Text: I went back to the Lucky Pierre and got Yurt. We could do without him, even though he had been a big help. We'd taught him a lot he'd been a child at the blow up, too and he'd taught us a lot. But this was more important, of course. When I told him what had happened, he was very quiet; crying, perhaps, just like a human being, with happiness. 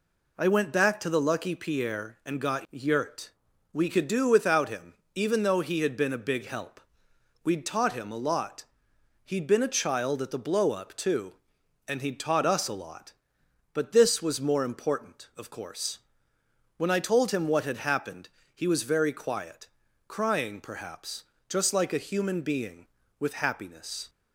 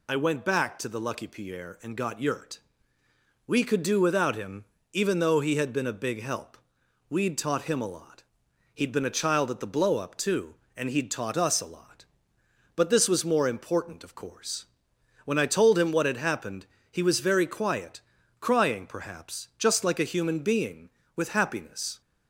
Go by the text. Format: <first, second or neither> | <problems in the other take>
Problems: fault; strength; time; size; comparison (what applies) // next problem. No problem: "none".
neither | pauses between "lot" and "he'd"; noticeable; the same in both